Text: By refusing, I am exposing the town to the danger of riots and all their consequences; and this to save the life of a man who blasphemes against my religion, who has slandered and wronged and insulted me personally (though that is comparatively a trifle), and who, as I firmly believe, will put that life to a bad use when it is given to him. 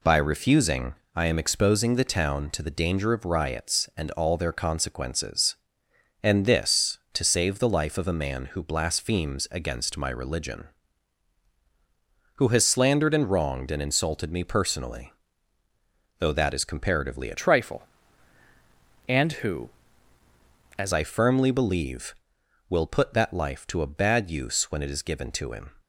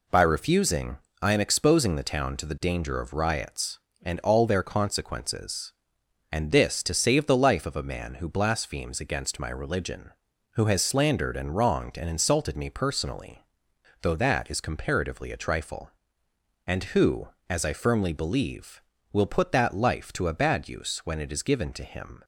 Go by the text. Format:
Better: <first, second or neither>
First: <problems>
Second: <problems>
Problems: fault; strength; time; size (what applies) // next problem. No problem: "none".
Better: second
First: changes voice from "trifle" to "as"; from 17.3 to 20.9 s; 3.6 s long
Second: none